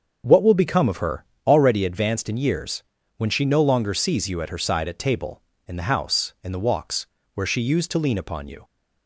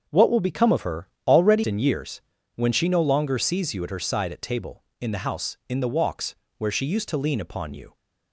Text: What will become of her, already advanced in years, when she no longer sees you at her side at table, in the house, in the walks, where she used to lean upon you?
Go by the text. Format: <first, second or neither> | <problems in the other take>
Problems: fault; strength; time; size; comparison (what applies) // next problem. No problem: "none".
first | starts louder than the rest; until 1.0 s; 6.5 dB; also in the first // skips "advanced"; at 1.6 s